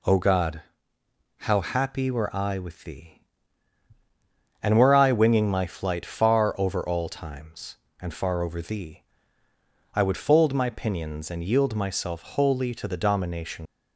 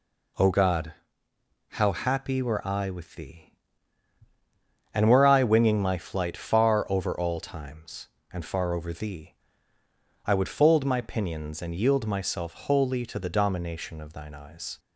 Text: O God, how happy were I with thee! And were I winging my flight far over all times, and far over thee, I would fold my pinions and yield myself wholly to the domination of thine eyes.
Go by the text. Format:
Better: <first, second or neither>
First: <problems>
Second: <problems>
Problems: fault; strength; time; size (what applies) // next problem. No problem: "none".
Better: second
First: stops before "of thine eyes"; at 13.6 s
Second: none